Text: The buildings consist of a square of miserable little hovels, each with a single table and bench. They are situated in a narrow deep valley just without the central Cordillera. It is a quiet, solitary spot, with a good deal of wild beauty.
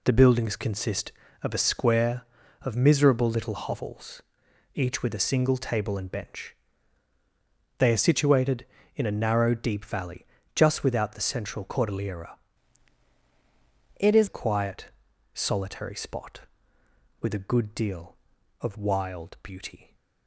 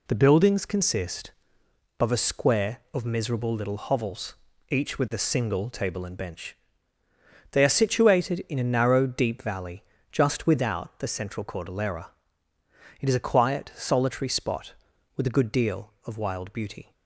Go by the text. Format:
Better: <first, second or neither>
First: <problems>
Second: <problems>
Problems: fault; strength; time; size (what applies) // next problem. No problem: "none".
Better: second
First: pauses between "valley" and "just"; slight; at 10.2 s; 0.30 s long // changes voice from "It" to "is"; from 13.9 to 14.2 s; 0.3 s long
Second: pauses between "valley" and "just"; slight; at 9.8 s; 0.30 s long